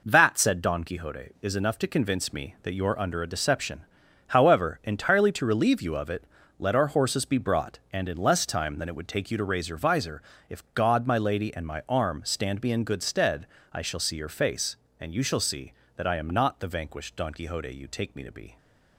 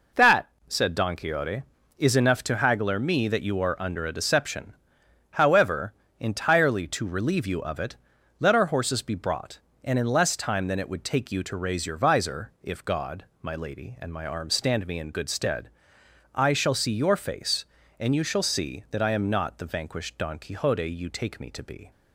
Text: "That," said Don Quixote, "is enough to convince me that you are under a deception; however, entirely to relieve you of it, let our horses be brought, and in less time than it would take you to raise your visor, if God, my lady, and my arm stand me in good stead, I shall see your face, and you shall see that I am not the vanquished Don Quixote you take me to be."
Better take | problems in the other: first | says "haggler" for "convince"; at 2.5 s

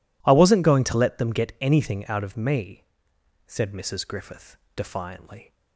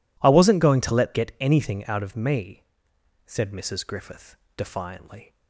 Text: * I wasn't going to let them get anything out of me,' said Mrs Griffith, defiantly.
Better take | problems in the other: first | skips "them"; at 1.1 s

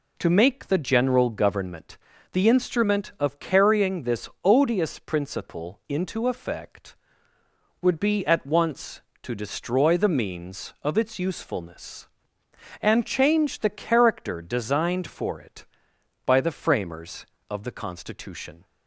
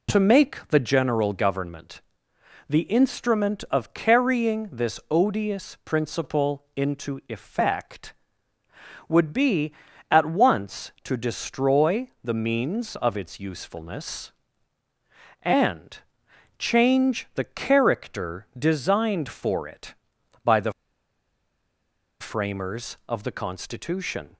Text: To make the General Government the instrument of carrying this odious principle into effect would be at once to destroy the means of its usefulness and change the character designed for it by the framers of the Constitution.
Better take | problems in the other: first | pauses between "Government" and "the"; noticeable; at 2.0 s; 0.66 s long; slight in the first // pauses between "and" and "change"; noticeable; at 15.9 s; 0.58 s long // pauses between "the" and "framers"; strong; at 20.7 s; 1.4 s long

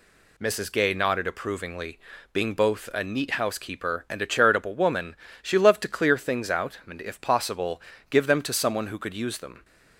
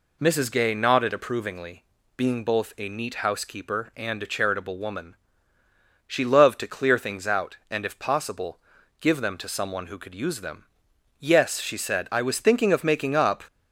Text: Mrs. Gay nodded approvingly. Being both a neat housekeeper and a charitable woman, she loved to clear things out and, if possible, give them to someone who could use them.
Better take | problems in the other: first | goes on to say "Yes she said I was thinking of making up"; strong; from 11.2 s on; 2.2 s long

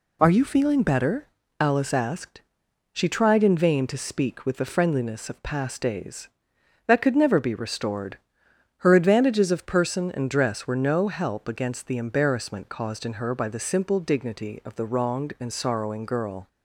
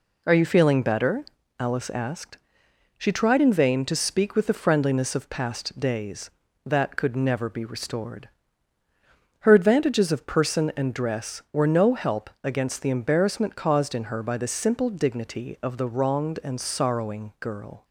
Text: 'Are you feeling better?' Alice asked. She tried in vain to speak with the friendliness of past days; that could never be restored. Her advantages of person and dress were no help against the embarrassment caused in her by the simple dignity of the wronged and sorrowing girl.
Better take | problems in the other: neither | none

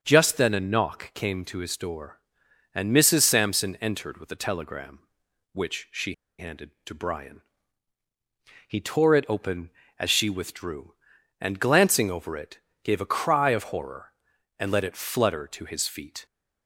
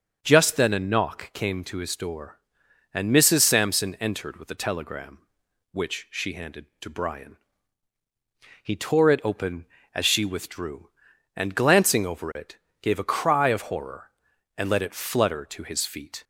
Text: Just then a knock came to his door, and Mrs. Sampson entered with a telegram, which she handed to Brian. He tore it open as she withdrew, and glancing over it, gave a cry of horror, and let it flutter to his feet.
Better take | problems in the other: second | starts louder than the rest; until 1.0 s; 7 dB; also in the second // pauses between "she" and "handed"; slight; at 6.1 s; 0.25 s long

